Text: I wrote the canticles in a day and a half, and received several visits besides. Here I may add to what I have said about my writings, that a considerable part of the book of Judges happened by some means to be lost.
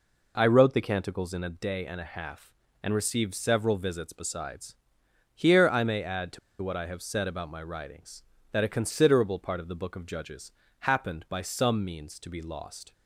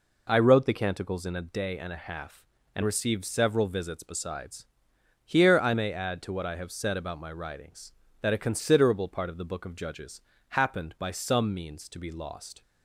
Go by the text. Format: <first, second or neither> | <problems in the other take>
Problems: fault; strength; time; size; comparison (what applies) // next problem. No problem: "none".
second | pauses between "to" and "what"; slight; at 6.3 s; 0.23 s long // pauses between "Judges" and "happened"; slight; at 10.5 s; 0.28 s long; slight in the second